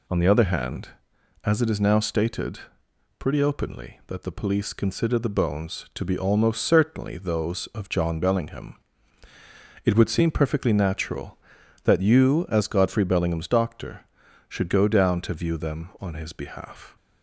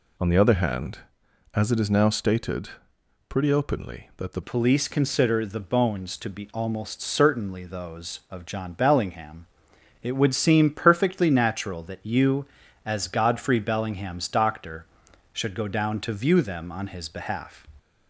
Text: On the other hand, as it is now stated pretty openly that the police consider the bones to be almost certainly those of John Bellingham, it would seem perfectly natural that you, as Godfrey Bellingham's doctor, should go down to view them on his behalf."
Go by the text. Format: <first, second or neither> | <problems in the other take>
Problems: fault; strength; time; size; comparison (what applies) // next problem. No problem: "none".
first | pauses between "stated" and "pretty"; noticeable; at 2.6 s; 0.60 s long; noticeable in the first // changes voice at "police"; from 4.4 s on; 13.2 s long